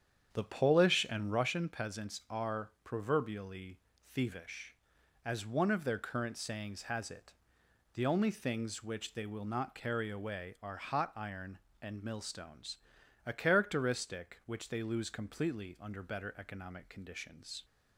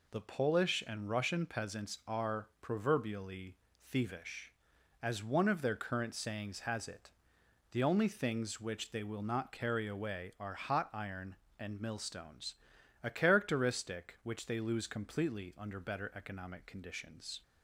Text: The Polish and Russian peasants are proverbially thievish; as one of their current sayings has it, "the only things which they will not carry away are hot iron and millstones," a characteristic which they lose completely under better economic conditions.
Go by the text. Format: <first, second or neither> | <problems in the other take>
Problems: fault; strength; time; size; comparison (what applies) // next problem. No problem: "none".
second | starts louder than the rest; strong; until 1.5 s; 8 dB // pauses between "proverbially" and "thievish"; slight; at 3.7 s; 0.30 s long; slight in the second